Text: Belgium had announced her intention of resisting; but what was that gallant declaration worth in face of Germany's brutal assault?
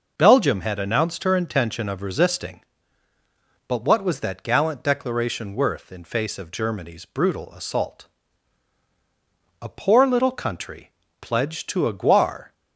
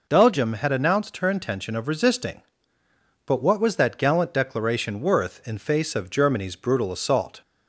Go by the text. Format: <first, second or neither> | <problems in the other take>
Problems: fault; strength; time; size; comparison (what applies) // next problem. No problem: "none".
second | goes on to say "A poor little country pledged to a guar"; strong; from 9.6 s on; 2.9 s long